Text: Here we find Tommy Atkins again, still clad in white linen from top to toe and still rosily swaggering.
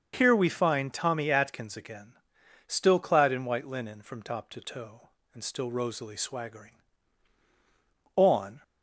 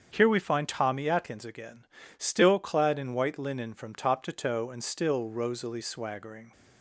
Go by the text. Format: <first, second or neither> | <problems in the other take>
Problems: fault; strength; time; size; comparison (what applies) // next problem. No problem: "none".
second | starts louder than the rest; until 1.1 s; 6.5 dB; strong in the second // goes on to say "On"; slight; from 8.1 s on; 0.48 s long